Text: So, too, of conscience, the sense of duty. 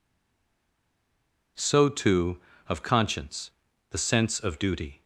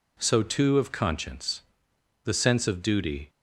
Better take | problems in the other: second | stays silent before the first word; noticeable; until 1.5 s; 1.5 s long

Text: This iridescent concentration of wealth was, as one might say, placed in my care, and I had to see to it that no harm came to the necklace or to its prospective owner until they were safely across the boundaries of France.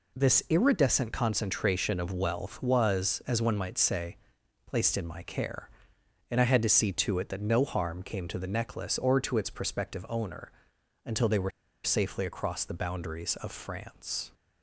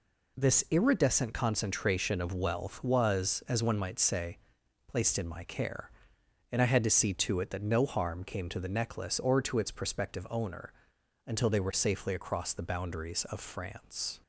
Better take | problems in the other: second | pauses between "owner" and "until"; noticeable; at 10.5 s; 0.52 s long; noticeable in the second // pauses between "were" and "safely"; slight; at 11.4 s; 0.34 s long

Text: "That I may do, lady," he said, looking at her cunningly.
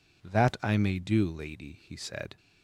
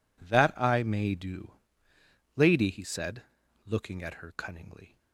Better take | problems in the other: second | stops before "looking at her cunningly"; at 2.3 s

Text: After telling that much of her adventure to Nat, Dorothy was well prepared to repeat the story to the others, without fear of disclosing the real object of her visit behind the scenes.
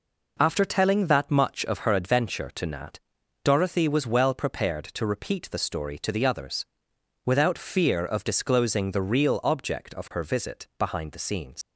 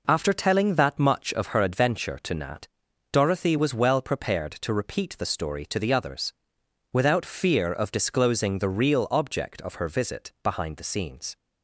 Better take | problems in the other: second | leaves "scenes" unfinished; at 11.6 s; 90 ms

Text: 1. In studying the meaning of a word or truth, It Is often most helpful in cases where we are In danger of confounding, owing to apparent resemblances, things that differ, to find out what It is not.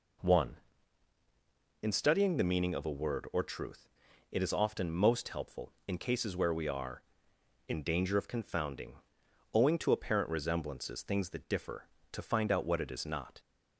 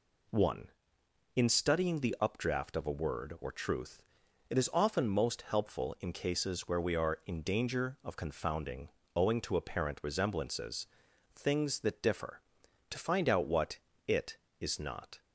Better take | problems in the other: first | says "updraft" for "meaning"; at 2.2 s // pauses between "what" and "It"; slight; at 13.7 s; 0.28 s long

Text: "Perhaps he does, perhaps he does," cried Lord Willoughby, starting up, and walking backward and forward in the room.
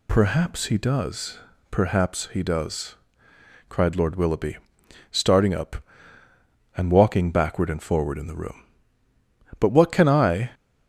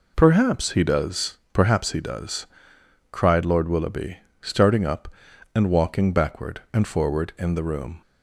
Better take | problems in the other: second | goes on to say "But what can I"; noticeable; from 9.5 s on; 0.94 s long

